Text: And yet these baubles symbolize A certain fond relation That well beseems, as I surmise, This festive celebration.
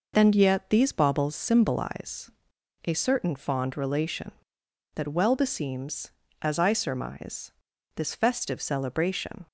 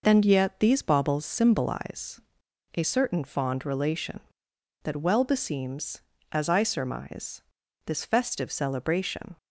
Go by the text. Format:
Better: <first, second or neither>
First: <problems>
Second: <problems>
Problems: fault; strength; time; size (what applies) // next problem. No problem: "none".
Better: neither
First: pauses between "symbolize" and "A"; noticeable; at 2.3 s; 0.54 s long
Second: pauses between "symbolize" and "A"; noticeable; at 2.2 s; 0.54 s long